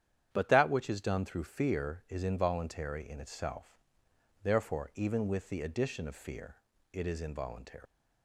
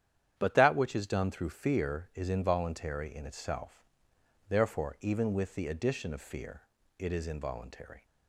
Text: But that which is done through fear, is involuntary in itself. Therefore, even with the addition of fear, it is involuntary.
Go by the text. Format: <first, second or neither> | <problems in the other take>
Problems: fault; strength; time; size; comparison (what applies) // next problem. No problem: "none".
second | starts louder than the rest; strong; until 1.3 s; 9.5 dB; strong in the second // leaves "involuntary" unfinished; at 7.8 s; 135 ms